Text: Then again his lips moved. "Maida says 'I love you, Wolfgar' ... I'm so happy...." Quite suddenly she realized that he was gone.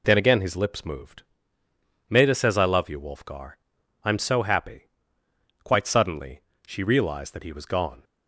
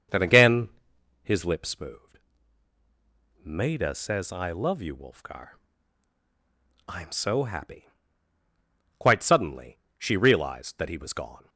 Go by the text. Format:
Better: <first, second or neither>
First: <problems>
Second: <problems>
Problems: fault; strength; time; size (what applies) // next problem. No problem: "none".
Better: first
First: pauses between "suddenly" and "she"; slight; at 6.4 s; 0.26 s long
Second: starts louder than the rest; until 1.4 s; 6.5 dB // pauses between "again" and "his"; noticeable; at 0.6 s; 0.54 s long // pauses between "suddenly" and "she"; slight; at 9.7 s; 0.22 s long